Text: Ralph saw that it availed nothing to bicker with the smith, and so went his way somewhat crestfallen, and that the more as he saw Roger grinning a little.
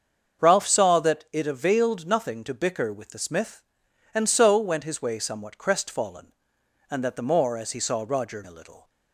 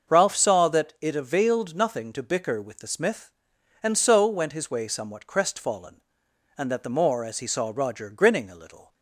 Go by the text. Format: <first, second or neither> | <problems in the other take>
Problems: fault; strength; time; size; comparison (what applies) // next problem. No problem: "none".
second | starts louder than the rest; until 1.4 s; 7 dB; also in the second // skips "grinning"; at 8.4 s